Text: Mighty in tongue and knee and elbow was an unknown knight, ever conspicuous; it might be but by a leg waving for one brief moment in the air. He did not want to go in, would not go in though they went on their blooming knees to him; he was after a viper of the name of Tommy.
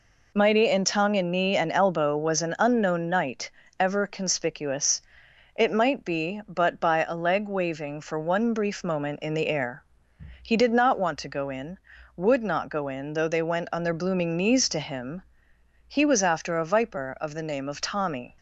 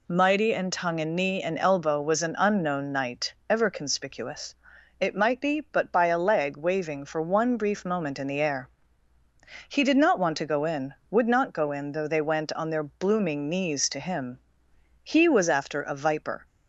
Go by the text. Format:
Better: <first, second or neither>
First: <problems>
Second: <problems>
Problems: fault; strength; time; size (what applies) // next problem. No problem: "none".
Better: first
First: none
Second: stops before "of the name of Tommy"; at 16.4 s